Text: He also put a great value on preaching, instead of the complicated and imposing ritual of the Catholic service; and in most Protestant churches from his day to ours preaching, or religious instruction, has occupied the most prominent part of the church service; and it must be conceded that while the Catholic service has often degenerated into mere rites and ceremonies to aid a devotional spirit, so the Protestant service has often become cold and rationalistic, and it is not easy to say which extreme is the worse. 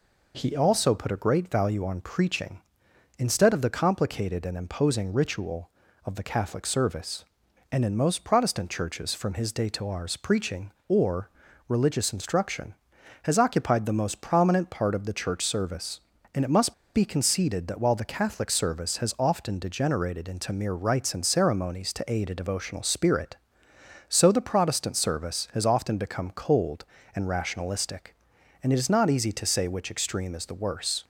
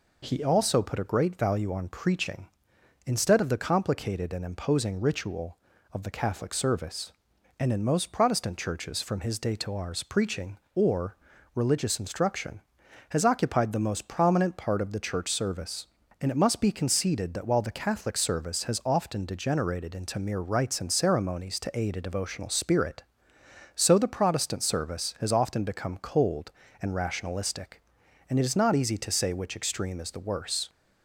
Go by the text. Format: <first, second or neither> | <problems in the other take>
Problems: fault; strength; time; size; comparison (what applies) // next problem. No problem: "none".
second | pauses between "or" and "religious"; at 11.2 s; 0.40 s long; also in the second // pauses between "must" and "be"; slight; at 16.7 s; 0.20 s long